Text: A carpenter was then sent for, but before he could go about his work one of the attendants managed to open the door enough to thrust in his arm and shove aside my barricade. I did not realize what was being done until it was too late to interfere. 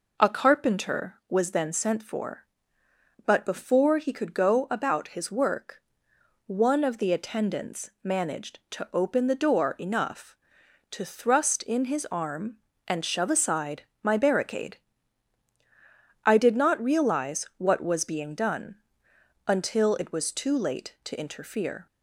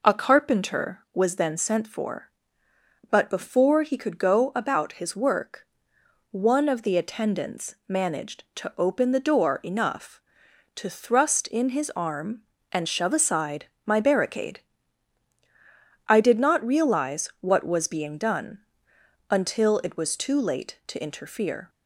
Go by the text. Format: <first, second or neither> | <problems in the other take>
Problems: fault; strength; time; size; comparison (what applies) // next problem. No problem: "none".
neither | pauses between "work" and "one"; noticeable; the same in both // pauses between "aside" and "my"; slight; the same in both // pauses between "done" and "until"; noticeable; the same in both